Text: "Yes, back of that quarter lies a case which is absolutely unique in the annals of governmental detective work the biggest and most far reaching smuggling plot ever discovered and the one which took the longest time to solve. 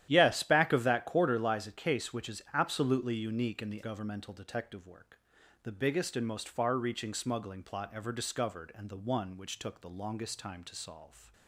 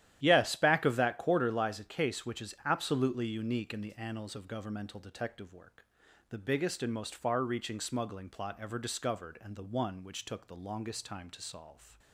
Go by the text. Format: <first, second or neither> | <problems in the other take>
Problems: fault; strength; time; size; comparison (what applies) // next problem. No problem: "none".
second | starts louder than the rest; strong; until 1.1 s; 11.5 dB; strong in the second // skips "annals of"; at 3.8 s // pauses between "work" and "the"; at 5.2 s; 0.42 s long; also in the second